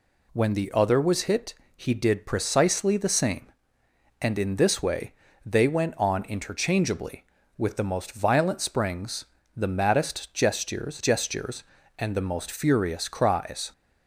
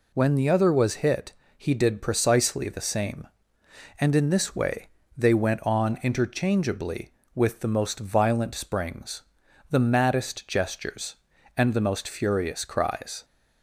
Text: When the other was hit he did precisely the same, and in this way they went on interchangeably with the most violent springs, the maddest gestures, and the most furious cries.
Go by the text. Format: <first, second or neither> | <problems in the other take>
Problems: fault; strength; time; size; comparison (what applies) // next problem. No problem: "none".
second | pauses between "hit" and "he"; slight; at 1.5 s; 0.22 s long; slight in the second // pauses between "way" and "they"; slight; at 5.1 s; 0.32 s long; slight in the second // says "gestures" twice; at 10.9 s